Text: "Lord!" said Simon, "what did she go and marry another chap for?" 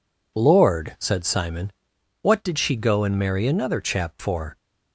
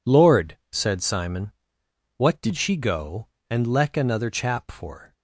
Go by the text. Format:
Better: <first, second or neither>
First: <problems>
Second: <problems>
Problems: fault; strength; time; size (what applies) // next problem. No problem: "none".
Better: first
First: none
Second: says "leck" for "marry"; at 3.6 s